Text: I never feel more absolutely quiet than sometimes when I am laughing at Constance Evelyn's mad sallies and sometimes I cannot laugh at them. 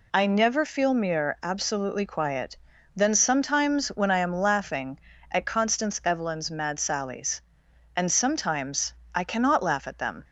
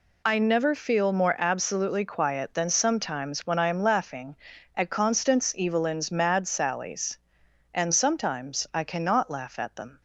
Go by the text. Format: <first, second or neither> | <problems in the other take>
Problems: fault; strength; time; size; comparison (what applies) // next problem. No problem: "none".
second | says "mere" for "more"; at 0.9 s // pauses between "sometimes" and "I"; slight; at 8.9 s; 0.22 s long